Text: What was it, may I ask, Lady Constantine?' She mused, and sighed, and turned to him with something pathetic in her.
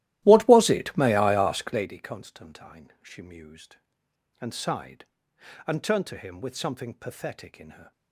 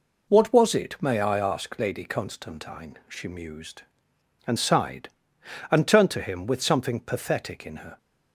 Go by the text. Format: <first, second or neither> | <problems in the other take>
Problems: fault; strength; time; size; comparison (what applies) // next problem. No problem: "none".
second | starts louder than the rest; strong; until 2.0 s; 15 dB